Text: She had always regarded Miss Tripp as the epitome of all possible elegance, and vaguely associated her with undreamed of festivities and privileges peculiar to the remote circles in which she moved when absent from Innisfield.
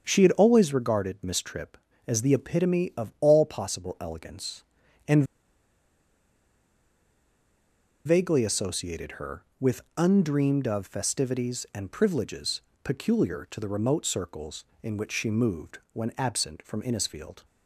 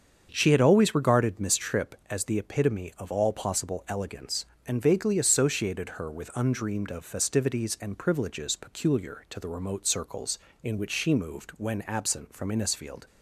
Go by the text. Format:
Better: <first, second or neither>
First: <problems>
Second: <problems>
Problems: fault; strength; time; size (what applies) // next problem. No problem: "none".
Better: second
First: starts louder than the rest; strong; until 1.1 s; 7 dB // pauses between "and" and "vaguely"; strong; at 5.2 s; 2.8 s long // pauses between "with" and "undreamed"; slight; at 9.8 s; 0.16 s long // pauses between "privileges" and "peculiar"; slight; at 12.6 s; 0.22 s long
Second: starts louder than the rest; strong; until 1.3 s; 7.5 dB